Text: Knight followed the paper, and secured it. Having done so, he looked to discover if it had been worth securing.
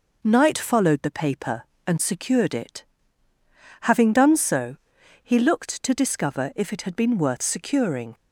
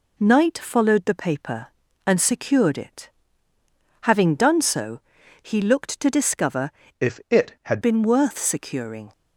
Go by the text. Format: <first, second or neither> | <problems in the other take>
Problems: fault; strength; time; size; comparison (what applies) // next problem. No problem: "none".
first | changes voice from "if" to "had"; from 6.9 to 7.7 s; 0.8 s long